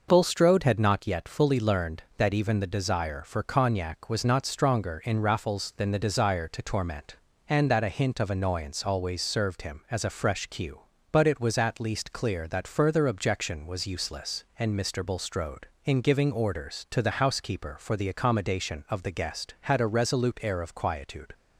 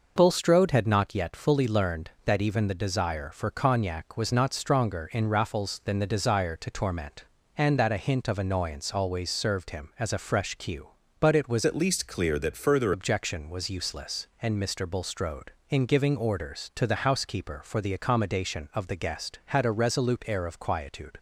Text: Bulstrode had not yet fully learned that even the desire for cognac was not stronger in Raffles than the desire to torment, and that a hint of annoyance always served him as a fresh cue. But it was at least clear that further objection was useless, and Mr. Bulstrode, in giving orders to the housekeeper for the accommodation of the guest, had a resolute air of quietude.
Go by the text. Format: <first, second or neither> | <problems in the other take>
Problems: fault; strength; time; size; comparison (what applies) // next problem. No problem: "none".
first | changes voice from "at" to "further"; from 11.6 to 12.9 s; 1.3 s long